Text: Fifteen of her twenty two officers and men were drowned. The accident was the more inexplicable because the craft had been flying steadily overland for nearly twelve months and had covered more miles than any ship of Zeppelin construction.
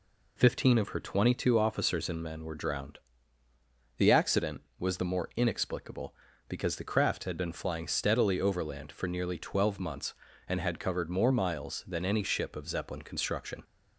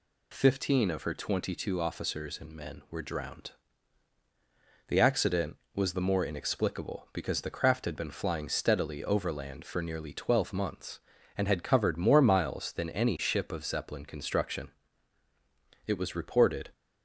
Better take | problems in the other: first | goes on to say "It was reported"; noticeable; from 15.8 s on; 0.86 s long

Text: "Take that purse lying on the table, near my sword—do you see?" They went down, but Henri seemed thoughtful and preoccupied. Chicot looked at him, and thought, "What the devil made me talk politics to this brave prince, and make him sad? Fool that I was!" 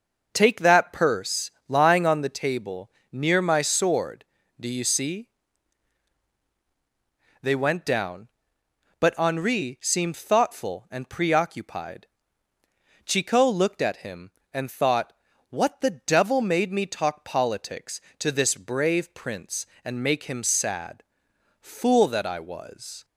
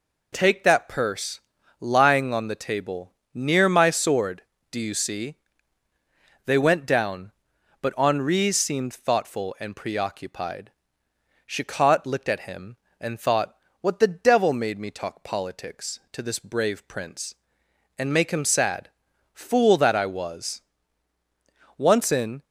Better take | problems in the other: first | pauses between "purse" and "lying"; at 1.3 s; 0.40 s long; slight in the first // goes on to say "Once in"; noticeable; from 21.7 s on; 0.66 s long

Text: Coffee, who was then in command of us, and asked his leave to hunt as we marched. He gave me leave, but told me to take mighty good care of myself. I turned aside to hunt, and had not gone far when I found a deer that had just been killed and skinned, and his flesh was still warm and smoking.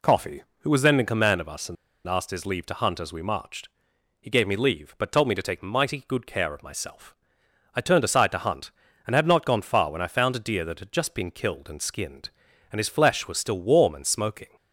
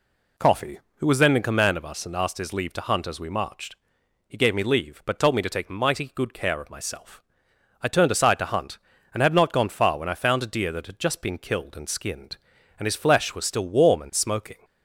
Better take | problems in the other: second | pauses between "and" and "asked"; slight; at 1.7 s; 0.32 s long

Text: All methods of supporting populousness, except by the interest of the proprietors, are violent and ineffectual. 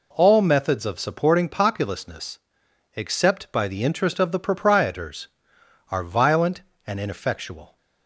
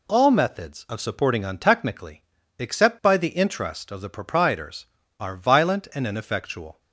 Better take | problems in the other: first | says "untechnically" for "populousness"; at 1.4 s

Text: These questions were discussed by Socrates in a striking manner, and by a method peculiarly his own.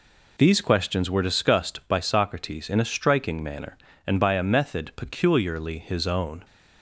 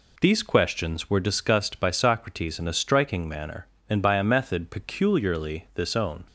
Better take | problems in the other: first | says "this" for "his"; at 5.7 s

